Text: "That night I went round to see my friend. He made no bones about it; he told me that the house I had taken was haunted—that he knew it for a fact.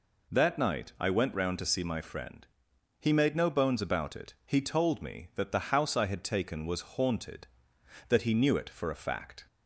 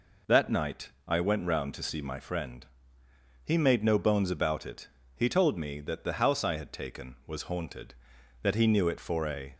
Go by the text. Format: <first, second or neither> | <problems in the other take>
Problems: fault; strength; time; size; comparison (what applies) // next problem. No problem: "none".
first | pauses between "night" and "I"; slight; at 0.8 s; 0.18 s long // stops before "fact"; at 9.5 s